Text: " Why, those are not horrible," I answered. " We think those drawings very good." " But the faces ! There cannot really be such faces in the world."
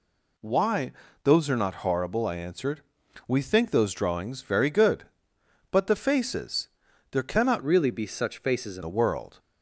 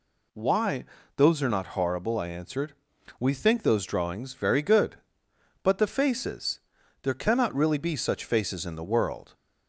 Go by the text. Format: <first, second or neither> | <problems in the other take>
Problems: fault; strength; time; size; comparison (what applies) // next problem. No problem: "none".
second | changes voice from "really" to "in"; from 7.6 to 8.8 s; 1.2 s long